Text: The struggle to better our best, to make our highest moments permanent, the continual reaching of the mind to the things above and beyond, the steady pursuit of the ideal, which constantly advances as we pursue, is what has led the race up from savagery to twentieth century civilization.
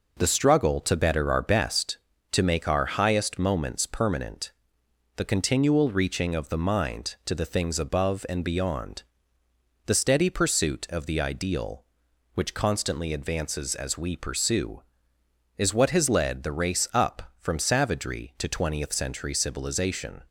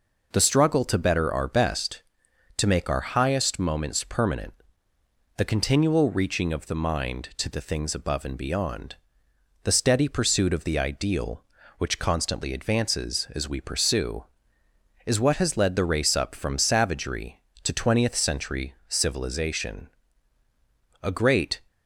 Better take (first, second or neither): first